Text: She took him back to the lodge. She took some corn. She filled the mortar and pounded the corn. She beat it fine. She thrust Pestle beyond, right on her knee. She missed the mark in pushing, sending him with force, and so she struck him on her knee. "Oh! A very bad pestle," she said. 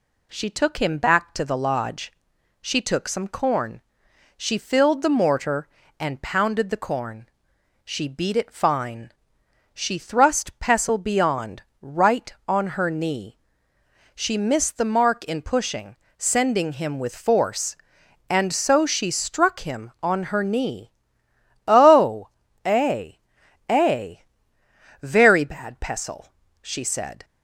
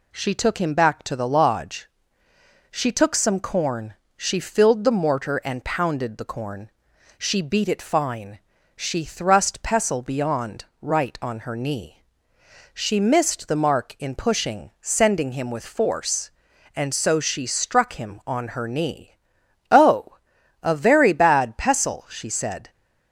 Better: second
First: says "A" twice; at 23.6 s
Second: none

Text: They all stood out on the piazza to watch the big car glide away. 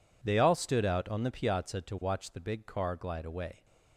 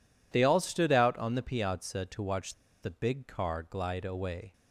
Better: first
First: none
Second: pauses between "watch" and "the"; slight; at 2.5 s; 0.28 s long

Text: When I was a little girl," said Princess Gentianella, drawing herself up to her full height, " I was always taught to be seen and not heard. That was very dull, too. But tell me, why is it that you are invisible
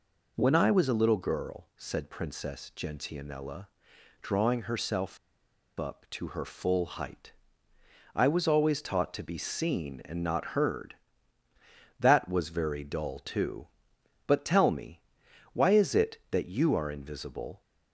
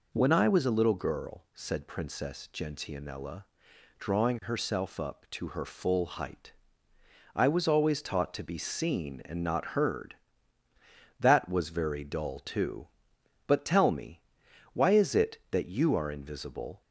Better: second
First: pauses between "herself" and "up"; noticeable; at 5.1 s; 0.62 s long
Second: none

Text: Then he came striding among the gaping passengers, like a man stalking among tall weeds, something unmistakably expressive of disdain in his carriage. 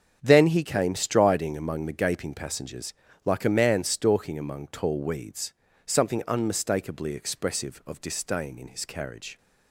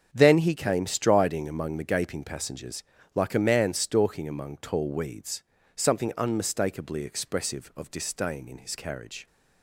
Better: neither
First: starts louder than the rest; strong; until 1.2 s; 7 dB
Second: starts louder than the rest; strong; until 1.1 s; 7 dB

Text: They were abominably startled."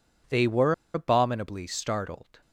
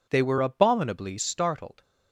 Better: second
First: pauses between "were" and "abominably"; slight; at 0.7 s; 0.21 s long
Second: none

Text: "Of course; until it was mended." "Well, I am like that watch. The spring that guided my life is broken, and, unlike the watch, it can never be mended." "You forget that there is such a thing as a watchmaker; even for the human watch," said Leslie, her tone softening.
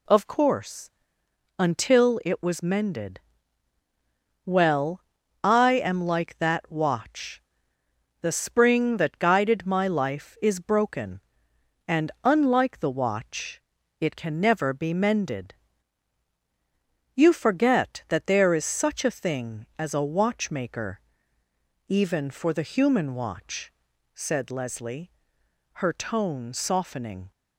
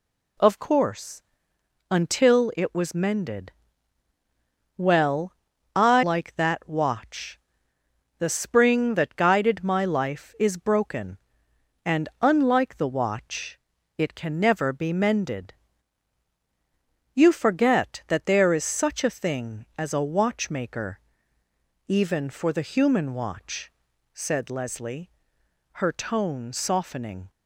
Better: first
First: none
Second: skips "am"; at 6.0 s

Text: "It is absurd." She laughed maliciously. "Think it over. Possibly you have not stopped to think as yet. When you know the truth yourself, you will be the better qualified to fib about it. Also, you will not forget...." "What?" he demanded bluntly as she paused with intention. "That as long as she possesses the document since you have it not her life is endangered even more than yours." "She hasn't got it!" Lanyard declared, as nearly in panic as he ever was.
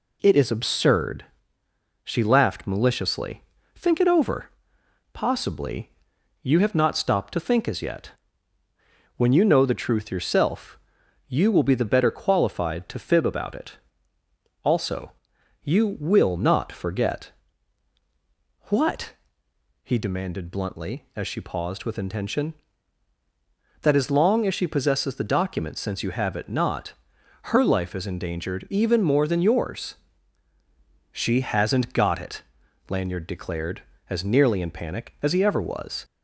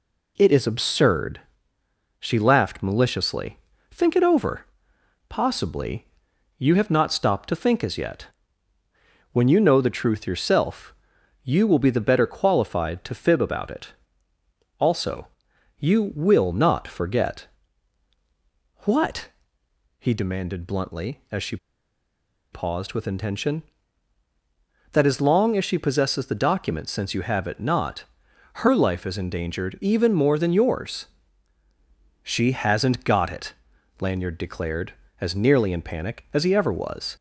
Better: first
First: pauses between "Possibly" and "you"; noticeable; at 5.9 s; 0.52 s long // pauses between "not" and "her"; noticeable; at 26.9 s; 0.50 s long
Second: pauses between "Possibly" and "you"; noticeable; at 6.0 s; 0.52 s long // pauses between "she" and "paused"; noticeable; at 21.5 s; 0.96 s long // pauses between "not" and "her"; noticeable; at 28.0 s; 0.50 s long

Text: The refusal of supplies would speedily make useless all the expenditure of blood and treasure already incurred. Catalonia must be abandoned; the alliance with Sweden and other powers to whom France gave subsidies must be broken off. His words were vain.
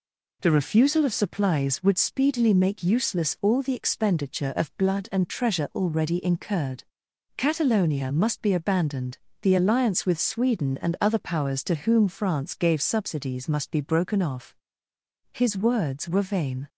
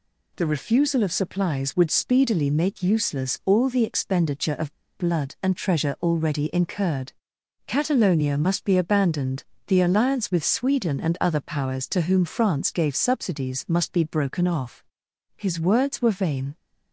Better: first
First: none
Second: pauses between "of" and "blood"; slight; at 4.7 s; 0.24 s long

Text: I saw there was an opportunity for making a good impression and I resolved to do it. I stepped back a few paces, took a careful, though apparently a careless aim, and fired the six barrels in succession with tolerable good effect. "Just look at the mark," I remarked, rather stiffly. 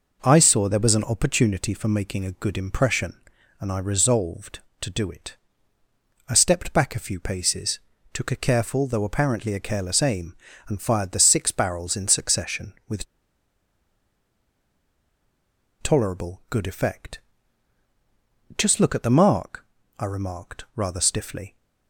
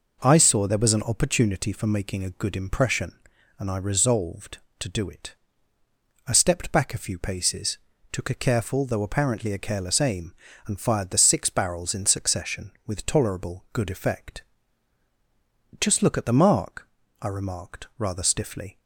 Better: second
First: pauses between "with" and "tolerable"; strong; at 13.0 s; 2.7 s long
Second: none

